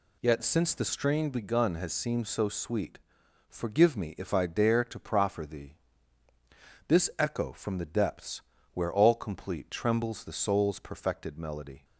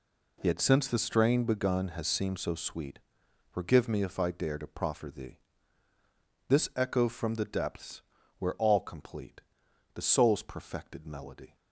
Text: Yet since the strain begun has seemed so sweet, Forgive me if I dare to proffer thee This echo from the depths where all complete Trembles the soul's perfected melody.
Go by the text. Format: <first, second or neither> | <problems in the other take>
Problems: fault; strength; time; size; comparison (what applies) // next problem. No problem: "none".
first | pauses between "thee" and "This"; at 5.3 s; 1.0 s long; also in the first // pauses between "depths" and "where"; slight; at 8.0 s; 0.36 s long; slight in the first // skips "Trembles"; at 9.6 s